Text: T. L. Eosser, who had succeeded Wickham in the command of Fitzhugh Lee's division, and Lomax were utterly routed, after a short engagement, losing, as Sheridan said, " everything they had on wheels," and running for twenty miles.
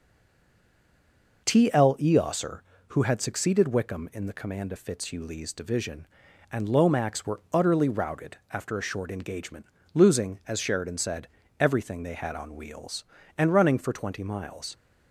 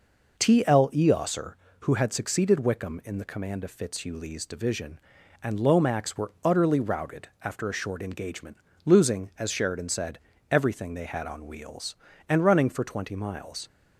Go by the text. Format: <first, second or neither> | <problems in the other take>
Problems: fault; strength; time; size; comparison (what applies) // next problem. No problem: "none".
second | stays silent before the first word; noticeable; until 1.4 s; 1.4 s long